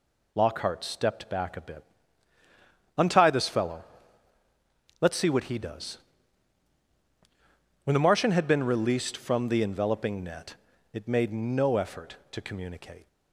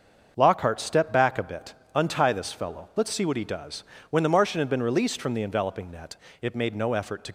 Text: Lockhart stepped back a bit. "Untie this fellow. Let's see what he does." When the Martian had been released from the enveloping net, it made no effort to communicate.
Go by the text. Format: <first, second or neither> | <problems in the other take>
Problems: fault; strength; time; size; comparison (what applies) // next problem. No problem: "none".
first | starts louder than the rest; until 1.3 s; 6.5 dB // stops before "communicate"; at 7.2 s